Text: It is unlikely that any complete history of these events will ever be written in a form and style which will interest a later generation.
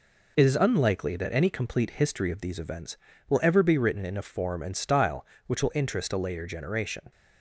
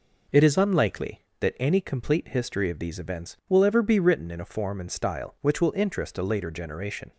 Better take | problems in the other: neither | none

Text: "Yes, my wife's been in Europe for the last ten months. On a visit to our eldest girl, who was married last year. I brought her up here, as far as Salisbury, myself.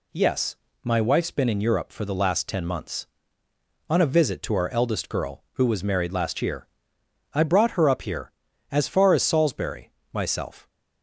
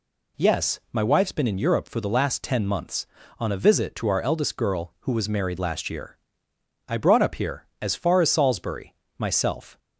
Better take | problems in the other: first | skips "her"; at 7.2 s

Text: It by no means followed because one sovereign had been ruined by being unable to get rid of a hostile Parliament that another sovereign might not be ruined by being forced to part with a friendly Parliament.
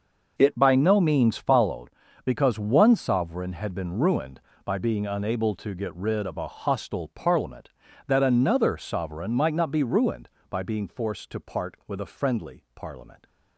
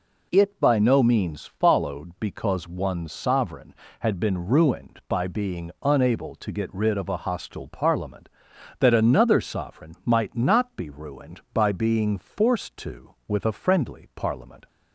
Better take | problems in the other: first | skips "part"; at 13.2 s

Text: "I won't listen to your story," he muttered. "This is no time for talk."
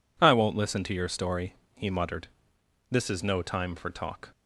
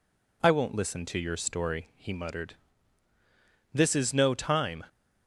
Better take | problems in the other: first | stops before "for talk"; at 4.8 s

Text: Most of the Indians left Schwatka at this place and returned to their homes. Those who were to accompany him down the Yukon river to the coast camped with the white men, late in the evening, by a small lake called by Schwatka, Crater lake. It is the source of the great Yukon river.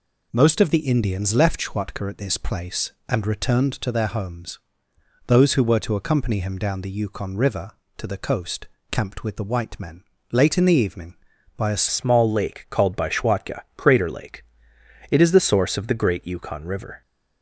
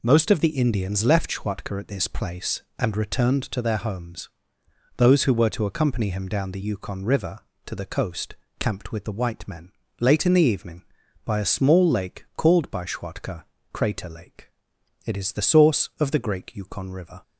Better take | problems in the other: second | pauses between "coast" and "camped"; slight; at 8.6 s; 0.24 s long; slight in the second // changes voice at "small"; from 11.8 s on; 5.2 s long

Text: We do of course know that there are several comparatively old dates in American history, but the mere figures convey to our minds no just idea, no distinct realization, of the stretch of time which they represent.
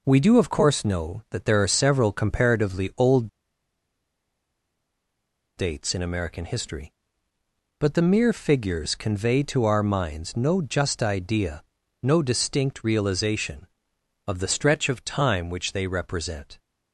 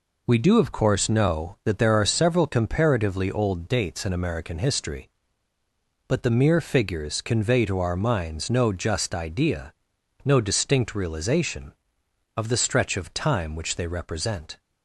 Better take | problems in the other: second | pauses between "old" and "dates"; strong; at 3.2 s; 2.3 s long

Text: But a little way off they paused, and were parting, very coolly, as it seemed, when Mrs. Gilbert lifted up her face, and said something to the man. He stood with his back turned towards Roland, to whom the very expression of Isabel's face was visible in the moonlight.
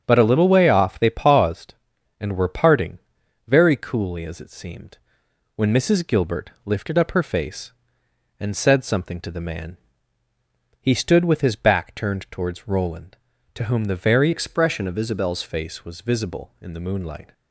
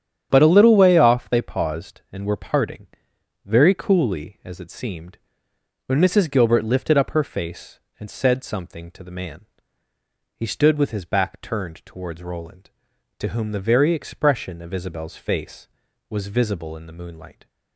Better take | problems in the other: second | starts louder than the rest; strong; until 1.0 s; 7.5 dB; strong in the second // changes voice from "expression" to "Isabel's"; from 14.3 to 15.4 s; 1.1 s long

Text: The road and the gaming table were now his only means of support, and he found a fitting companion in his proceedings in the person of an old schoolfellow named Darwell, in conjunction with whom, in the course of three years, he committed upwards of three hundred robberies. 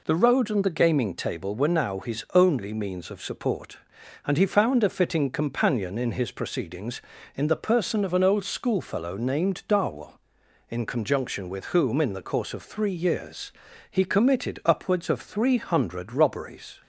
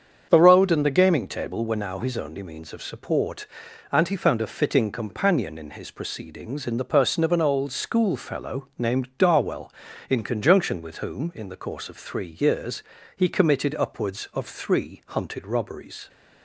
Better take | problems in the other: first | starts louder than the rest; strong; until 1.3 s; 7.5 dB // says "hunted" for "hundred"; at 15.0 s

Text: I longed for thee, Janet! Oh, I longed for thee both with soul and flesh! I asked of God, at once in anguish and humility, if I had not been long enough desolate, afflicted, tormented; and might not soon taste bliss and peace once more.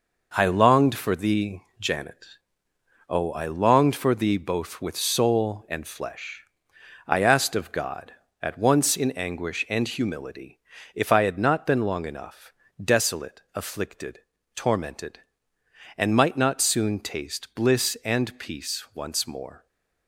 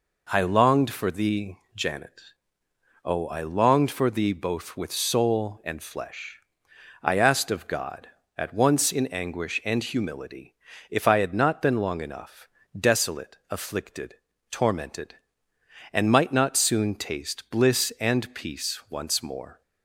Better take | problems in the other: second | gets quieter; throughout; 6.5 dB // pauses between "enough" and "desolate"; slight; at 12.5 s; 0.30 s long; slight in the second // stays silent after the last word; slight; from 19.5 s on; 0.5 s long

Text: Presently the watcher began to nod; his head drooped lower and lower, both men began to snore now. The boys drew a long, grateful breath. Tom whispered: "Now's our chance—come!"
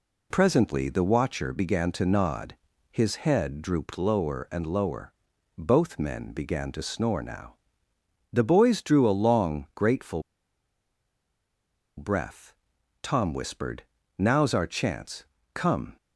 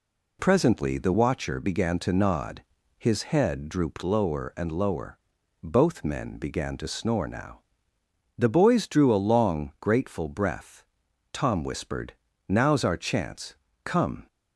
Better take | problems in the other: second | pauses between "grateful" and "breath"; strong; at 10.2 s; 1.7 s long

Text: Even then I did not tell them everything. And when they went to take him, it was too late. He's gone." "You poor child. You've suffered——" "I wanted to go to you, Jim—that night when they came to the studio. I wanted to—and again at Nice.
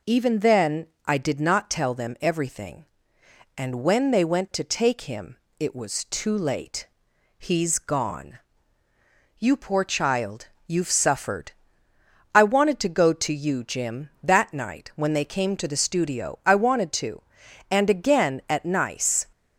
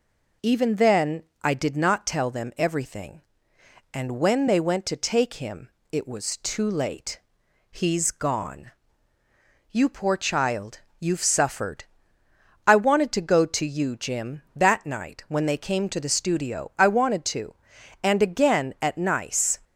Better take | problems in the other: neither | pauses between "then" and "I"; slight; the same in both

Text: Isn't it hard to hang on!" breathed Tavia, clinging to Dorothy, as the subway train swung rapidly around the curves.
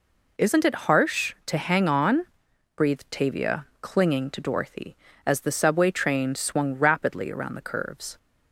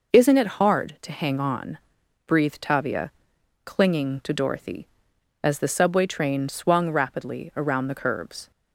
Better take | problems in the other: second | says "harsh" for "hard"; at 0.7 s

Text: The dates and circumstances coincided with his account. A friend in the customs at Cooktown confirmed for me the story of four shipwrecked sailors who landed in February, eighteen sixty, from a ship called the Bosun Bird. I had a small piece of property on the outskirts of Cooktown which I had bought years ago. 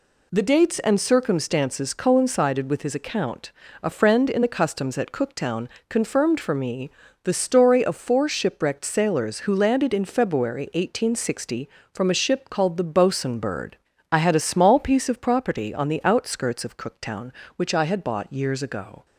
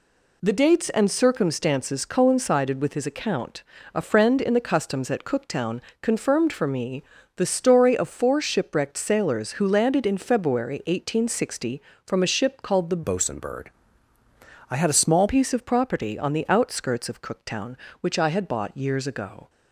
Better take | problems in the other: first | pauses between "Cooktown" and "confirmed"; slight; at 5.8 s; 0.18 s long; slight in the first // pauses between "me" and "the"; slight; at 7.0 s; 0.34 s long; slight in the first // changes voice from "Bosun" to "small"; from 13.0 to 15.2 s; 2.2 s long

